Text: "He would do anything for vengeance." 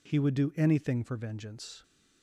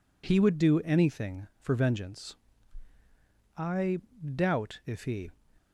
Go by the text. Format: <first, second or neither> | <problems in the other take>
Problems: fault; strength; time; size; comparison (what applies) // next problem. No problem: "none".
first | goes on to say "I doubt if he"; strong; from 3.5 s on; 1.7 s long